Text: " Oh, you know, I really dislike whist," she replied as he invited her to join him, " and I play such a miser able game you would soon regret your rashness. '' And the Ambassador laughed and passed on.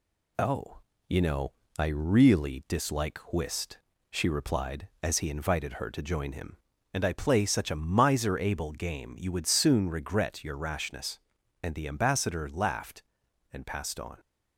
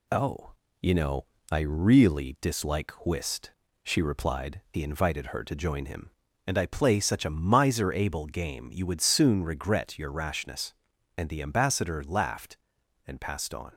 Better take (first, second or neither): first